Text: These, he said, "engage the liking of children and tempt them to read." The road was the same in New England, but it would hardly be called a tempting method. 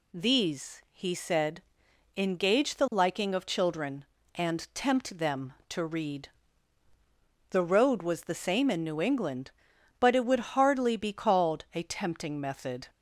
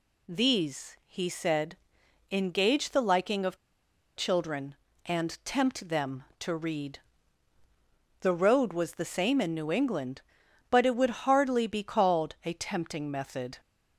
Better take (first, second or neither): first